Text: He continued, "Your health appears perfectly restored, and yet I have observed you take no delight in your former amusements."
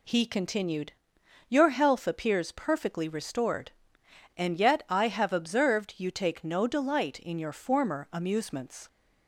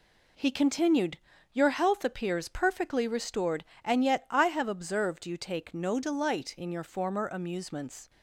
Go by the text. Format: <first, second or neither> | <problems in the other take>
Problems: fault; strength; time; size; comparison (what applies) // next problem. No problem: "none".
neither | none